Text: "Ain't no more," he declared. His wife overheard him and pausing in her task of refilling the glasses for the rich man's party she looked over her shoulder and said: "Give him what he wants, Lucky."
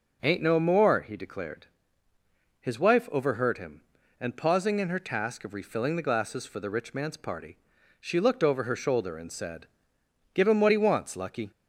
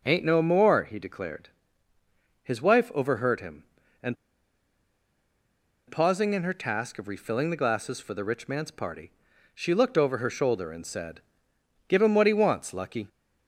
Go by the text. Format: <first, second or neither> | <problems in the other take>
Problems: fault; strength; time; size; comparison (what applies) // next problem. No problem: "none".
first | pauses between "and" and "pausing"; strong; at 4.1 s; 1.7 s long // pauses between "party" and "she"; noticeable; at 9.0 s; 0.46 s long; noticeable in the first